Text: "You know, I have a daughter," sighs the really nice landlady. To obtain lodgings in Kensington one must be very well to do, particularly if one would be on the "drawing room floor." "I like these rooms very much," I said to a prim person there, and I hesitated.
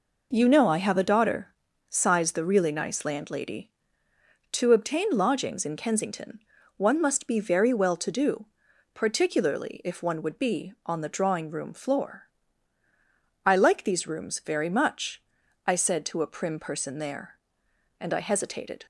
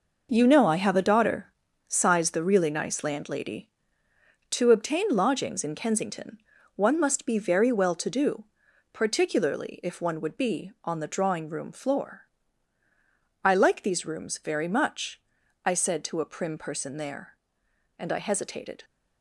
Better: first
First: pauses between "Kensington" and "one"; at 6.3 s; 0.38 s long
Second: gets quieter; strong; throughout; 9.5 dB // pauses between "Kensington" and "one"; at 6.3 s; 0.38 s long

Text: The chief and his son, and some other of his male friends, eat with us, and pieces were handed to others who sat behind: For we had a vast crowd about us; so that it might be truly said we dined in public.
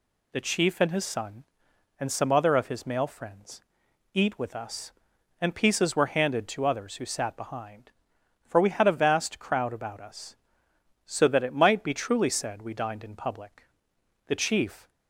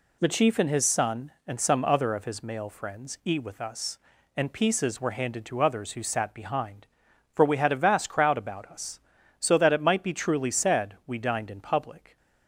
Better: second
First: goes on to say "The chief"; noticeable; from 14.2 s on; 0.64 s long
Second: none

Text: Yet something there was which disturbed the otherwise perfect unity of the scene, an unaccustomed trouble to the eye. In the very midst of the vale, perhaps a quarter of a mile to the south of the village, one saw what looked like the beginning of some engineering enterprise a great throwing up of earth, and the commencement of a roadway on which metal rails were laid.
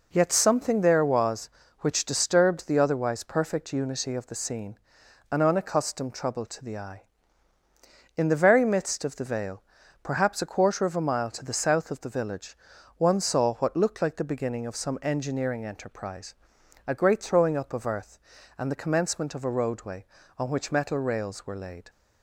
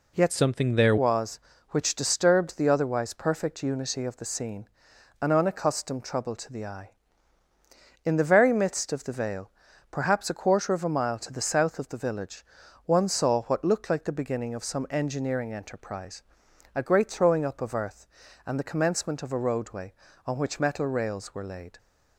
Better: first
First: pauses between "enterprise" and "a"; noticeable; at 16.3 s; 0.52 s long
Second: changes voice from "something" to "there"; from 0.3 to 0.9 s; 0.6 s long // pauses between "enterprise" and "a"; noticeable; at 16.2 s; 0.52 s long

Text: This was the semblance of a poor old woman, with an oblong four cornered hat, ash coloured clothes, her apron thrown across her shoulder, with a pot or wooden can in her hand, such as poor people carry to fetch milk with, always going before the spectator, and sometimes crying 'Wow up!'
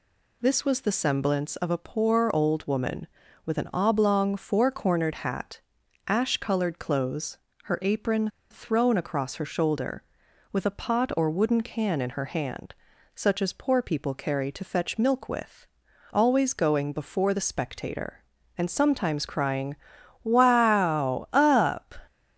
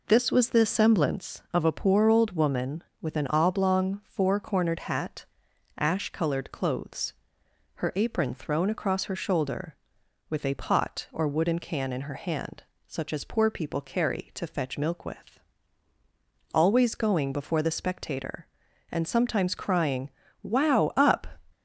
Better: second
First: pauses between "apron" and "thrown"; slight; at 8.2 s; 0.21 s long // pauses between "crying" and "Wow"; noticeable; at 19.7 s; 0.48 s long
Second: pauses between "crying" and "Wow"; slight; at 20.0 s; 0.32 s long

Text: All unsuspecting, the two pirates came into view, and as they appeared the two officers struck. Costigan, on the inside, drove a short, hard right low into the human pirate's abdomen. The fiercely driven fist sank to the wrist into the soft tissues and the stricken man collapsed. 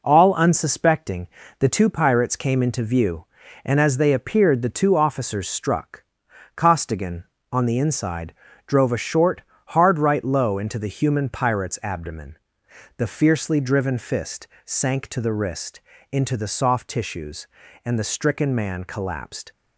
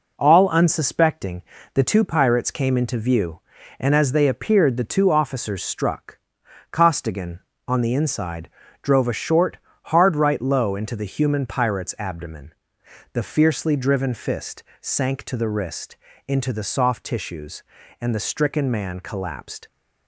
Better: neither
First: pauses between "fist" and "sank"; slight; at 14.4 s; 0.18 s long // pauses between "wrist" and "into"; slight; at 15.8 s; 0.30 s long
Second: pauses between "fist" and "sank"; slight; at 14.6 s; 0.18 s long // pauses between "wrist" and "into"; slight; at 15.9 s; 0.30 s long

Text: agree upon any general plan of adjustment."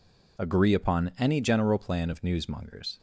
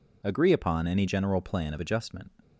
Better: second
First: says "newsmongers" for "adjustment"; at 2.2 s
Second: none

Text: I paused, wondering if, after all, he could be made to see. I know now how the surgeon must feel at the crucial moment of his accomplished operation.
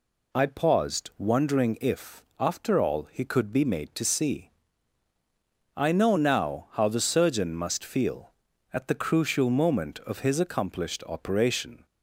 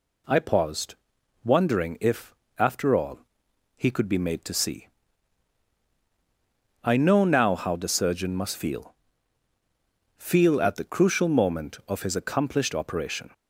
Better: first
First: none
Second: says "feel" twice; at 10.1 s

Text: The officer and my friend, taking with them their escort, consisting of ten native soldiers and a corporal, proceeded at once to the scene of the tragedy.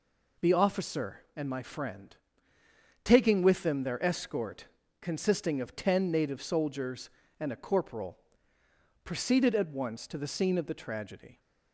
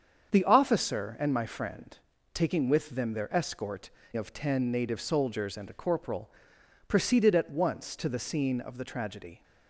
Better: first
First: none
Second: starts louder than the rest; strong; until 1.3 s; 7.5 dB // skips "consisting"; at 4.0 s

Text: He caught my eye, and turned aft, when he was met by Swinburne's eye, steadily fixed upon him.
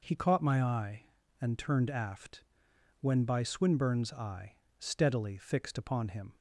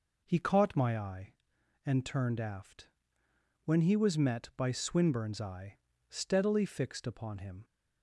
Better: second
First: skips "he was met"; at 3.2 s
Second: none

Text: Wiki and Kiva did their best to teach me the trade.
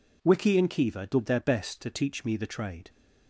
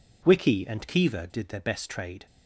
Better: first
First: none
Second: skips "to teach me the"; at 1.8 s

